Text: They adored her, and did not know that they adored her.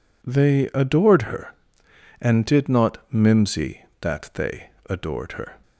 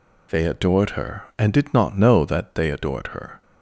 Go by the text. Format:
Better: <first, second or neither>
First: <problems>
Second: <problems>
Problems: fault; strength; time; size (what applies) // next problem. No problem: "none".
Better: second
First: says "mimsy" for "know"; at 3.1 s // pauses between "they" and "adored"; slight; at 4.6 s; 0.18 s long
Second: none